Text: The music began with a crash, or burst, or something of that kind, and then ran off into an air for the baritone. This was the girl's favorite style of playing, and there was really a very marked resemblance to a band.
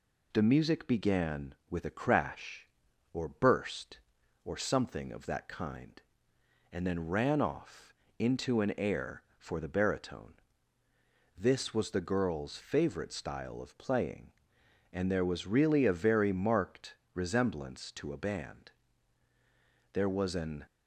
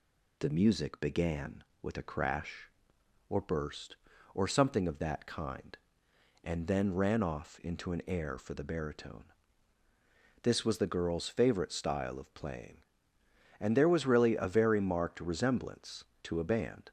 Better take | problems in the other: second | pauses between "off" and "into"; slight; at 7.9 s; 0.24 s long // pauses between "marked" and "resemblance"; slight; at 16.9 s; 0.18 s long // goes on to say "There was an"; noticeable; from 19.9 s on; 0.70 s long

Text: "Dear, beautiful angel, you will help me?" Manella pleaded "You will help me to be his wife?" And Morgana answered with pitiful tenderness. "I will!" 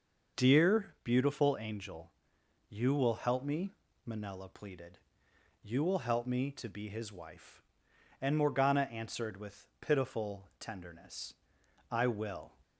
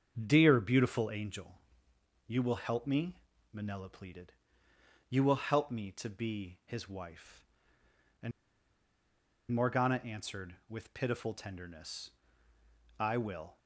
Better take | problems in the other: first | starts louder than the rest; until 1.1 s; 7 dB // pauses between "pleaded" and "You"; noticeable; at 4.3 s; 0.78 s long; noticeable in the first // pauses between "And" and "Morgana"; at 8.3 s; 1.2 s long

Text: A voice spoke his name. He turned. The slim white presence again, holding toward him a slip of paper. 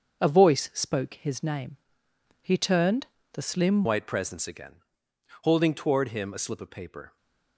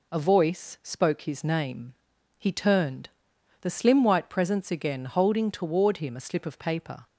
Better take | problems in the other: second | starts louder than the rest; until 1.2 s; 6.5 dB // changes voice at "white"; from 3.8 s on; 3.3 s long

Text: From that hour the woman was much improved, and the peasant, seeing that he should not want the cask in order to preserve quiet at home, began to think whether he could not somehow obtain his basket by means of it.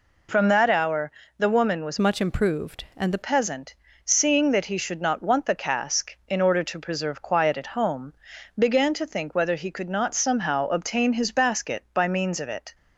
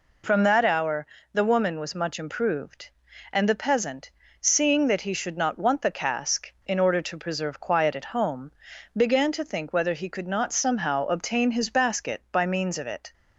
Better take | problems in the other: second | pauses between "hour" and "the"; slight; at 1.0 s; 0.30 s long; slight in the second // changes voice from "much" to "the"; from 1.9 to 3.2 s; 1.3 s long

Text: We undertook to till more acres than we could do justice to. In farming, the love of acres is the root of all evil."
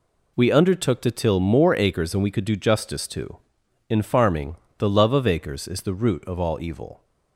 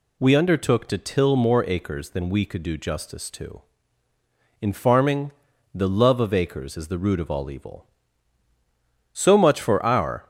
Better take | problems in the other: first | goes on to say "So much for our"; noticeable; from 9.1 s on; 1.1 s long

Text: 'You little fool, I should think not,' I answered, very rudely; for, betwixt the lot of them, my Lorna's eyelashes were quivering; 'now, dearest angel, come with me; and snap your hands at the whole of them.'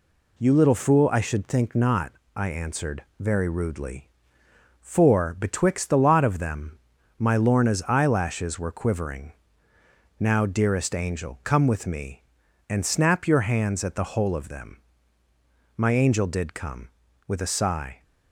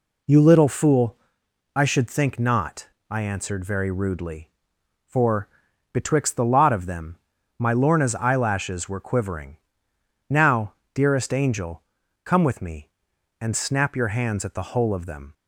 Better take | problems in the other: second | goes on to say "My angel did come with a sigh"; strong; from 15.7 s on; 2.2 s long

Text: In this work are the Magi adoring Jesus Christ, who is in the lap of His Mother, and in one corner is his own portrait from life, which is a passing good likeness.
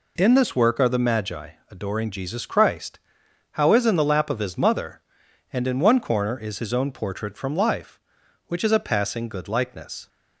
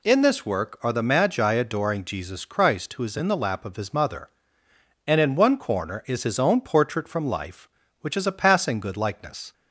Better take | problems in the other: second | pauses between "Magi" and "adoring"; slight; at 1.4 s; 0.20 s long // says "how" for "who"; at 3.5 s

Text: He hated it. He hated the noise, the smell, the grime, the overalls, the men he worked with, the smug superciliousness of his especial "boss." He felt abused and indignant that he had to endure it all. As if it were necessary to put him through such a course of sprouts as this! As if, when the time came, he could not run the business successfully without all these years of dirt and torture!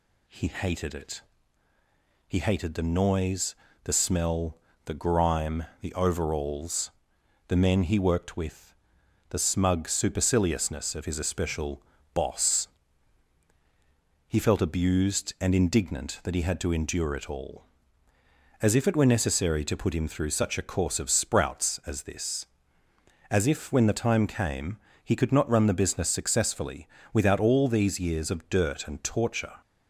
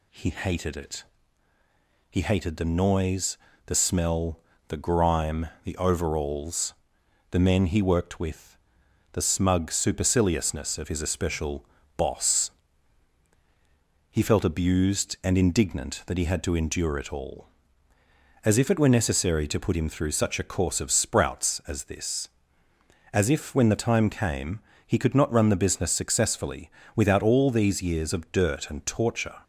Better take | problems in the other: neither | pauses between "especial" and "boss"; slight; the same in both // pauses between "successfully" and "without"; slight; the same in both

